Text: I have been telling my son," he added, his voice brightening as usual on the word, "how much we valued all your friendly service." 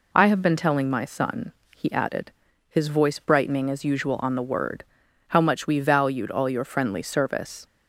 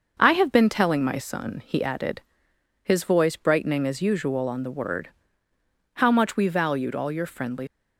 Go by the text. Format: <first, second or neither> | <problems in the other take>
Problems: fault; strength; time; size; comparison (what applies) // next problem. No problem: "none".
first | starts louder than the rest; until 1.1 s; 6 dB // stops before "service"; at 7.6 s